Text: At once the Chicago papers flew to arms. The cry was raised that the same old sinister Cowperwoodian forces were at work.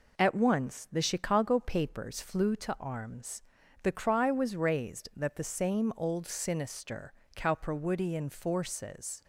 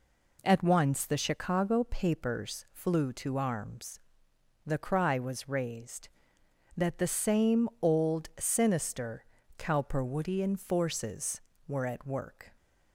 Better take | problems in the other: second | pauses between "sinister" and "Cowperwoodian"; slight; at 7.1 s; 0.24 s long; slight in the second // stops before "were at work"; at 9.2 s

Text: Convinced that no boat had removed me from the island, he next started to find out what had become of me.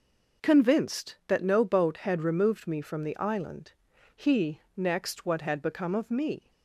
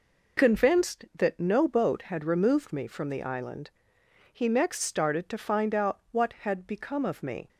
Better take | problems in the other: second | skips "started to find out"; at 5.2 s

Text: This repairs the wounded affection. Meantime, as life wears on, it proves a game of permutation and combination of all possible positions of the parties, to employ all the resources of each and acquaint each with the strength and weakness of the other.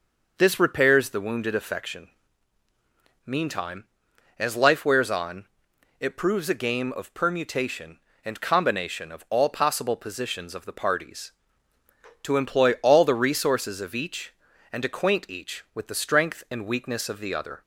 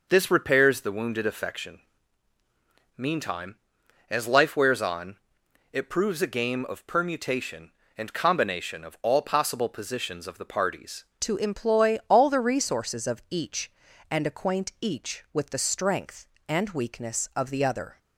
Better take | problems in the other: first | changes voice at "to"; from 11.1 s on; 6.8 s long

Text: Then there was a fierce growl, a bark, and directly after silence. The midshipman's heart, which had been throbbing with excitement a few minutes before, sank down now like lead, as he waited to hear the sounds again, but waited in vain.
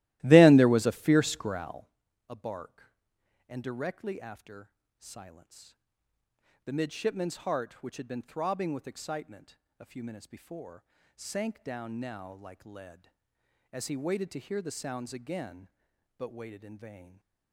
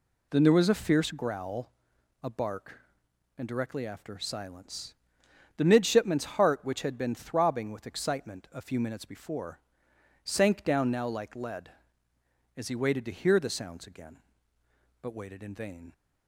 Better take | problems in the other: second | starts louder than the rest; strong; until 1.9 s; 16.5 dB // pauses between "after" and "silence"; slight; at 4.6 s; 0.28 s long // pauses between "excitement" and "a"; slight; at 9.5 s; 0.24 s long

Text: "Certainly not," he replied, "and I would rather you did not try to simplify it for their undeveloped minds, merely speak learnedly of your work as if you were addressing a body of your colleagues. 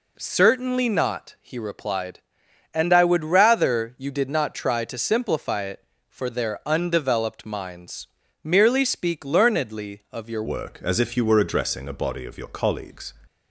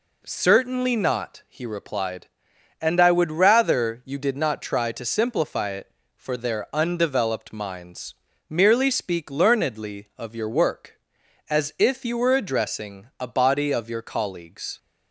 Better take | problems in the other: second | changes voice at "work"; from 10.4 s on; 2.7 s long

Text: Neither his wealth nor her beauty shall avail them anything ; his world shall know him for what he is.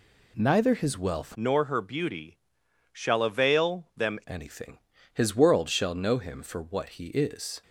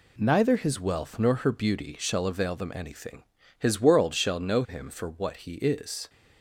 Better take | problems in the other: second | changes voice from "nor" to "them"; from 1.3 to 4.1 s; 2.8 s long // pauses between "beauty" and "shall"; noticeable; at 2.3 s; 0.54 s long

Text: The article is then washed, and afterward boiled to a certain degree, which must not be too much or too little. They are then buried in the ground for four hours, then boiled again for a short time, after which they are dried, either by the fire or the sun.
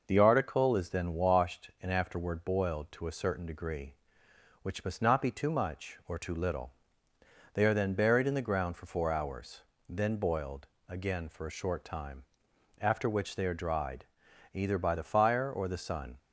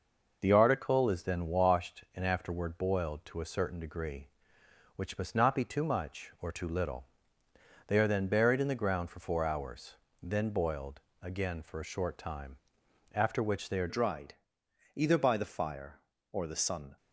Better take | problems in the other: first | pauses between "boiled" and "again"; slight; at 10.9 s; 0.22 s long; slight in the first // changes voice at "dried"; from 13.8 s on; 3.1 s long

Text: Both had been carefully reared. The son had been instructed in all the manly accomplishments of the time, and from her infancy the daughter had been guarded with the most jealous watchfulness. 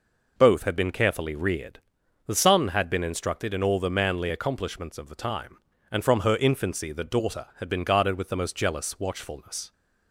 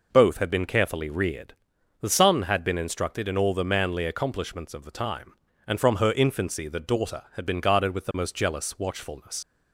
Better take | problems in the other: first | leaves "watchfulness" unfinished; at 9.4 s; 85 ms

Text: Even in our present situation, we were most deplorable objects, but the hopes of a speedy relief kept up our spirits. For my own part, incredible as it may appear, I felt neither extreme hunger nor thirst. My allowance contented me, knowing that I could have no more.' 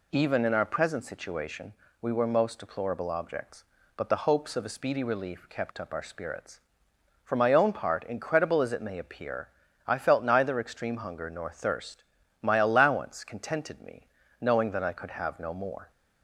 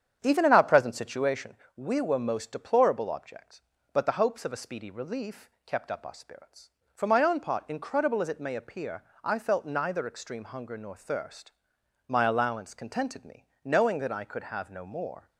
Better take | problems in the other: first | starts louder than the rest; strong; until 1.5 s; 8 dB // pauses between "relief" and "kept"; slight; at 5.4 s; 0.16 s long

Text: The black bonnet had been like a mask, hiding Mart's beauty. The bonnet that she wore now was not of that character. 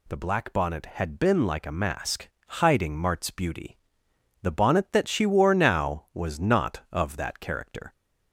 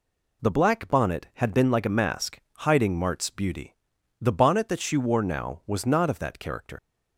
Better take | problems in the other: first | leaves "character" unfinished; at 6.7 s; 105 ms

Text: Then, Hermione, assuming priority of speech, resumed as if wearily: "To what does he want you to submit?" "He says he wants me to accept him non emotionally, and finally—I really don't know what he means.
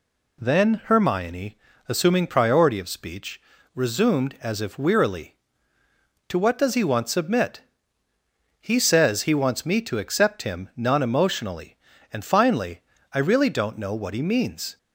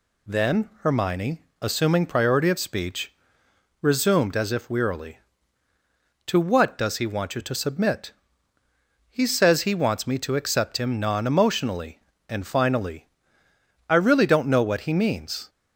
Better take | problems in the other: second | skips "you to"; at 7.0 s

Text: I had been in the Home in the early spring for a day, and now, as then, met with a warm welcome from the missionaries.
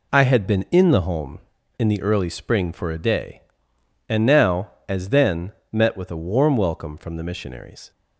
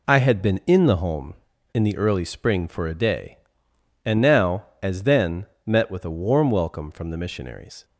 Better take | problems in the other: neither | none

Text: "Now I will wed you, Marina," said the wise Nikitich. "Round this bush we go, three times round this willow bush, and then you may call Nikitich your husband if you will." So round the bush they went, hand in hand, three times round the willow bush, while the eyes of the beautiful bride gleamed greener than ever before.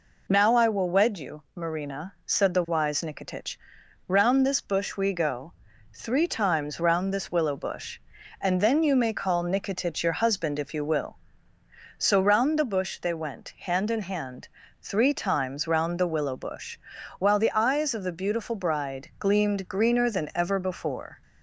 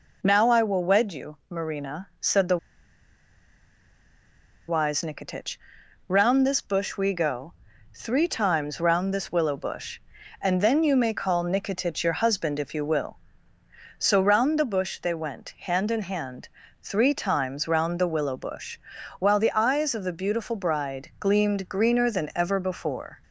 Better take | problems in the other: first | pauses between "the" and "wise"; strong; at 2.5 s; 2.0 s long

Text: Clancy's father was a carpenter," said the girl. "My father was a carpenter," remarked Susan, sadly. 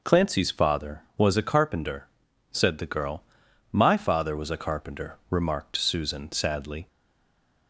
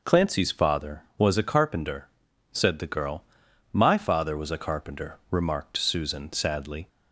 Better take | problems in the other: second | stays silent after the last word; slight; from 6.8 s on; 0.8 s long

